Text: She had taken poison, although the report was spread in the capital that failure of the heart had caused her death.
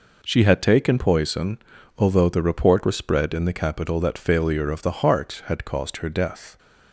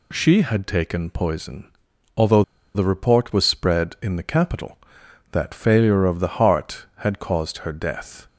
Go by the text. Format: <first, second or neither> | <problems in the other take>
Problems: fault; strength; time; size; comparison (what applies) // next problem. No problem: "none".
first | pauses between "although" and "the"; slight; at 2.4 s; 0.33 s long